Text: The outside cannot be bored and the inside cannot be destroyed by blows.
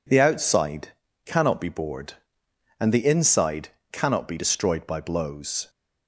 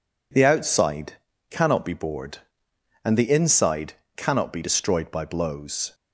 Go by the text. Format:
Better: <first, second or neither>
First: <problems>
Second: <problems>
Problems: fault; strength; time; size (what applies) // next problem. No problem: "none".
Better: neither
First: pauses between "outside" and "cannot"; slight; at 0.9 s; 0.34 s long // pauses between "inside" and "cannot"; slight; at 3.6 s; 0.24 s long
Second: pauses between "outside" and "cannot"; slight; at 1.1 s; 0.34 s long // pauses between "inside" and "cannot"; slight; at 3.9 s; 0.24 s long